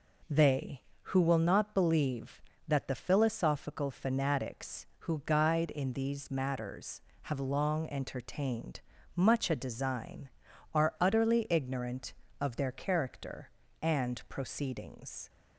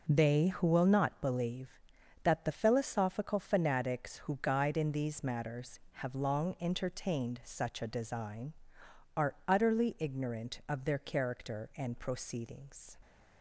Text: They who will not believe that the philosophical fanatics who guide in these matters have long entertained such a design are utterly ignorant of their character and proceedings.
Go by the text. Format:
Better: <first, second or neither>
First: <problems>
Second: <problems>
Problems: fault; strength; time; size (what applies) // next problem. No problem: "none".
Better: second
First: says "much" for "such"; at 9.1 s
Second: none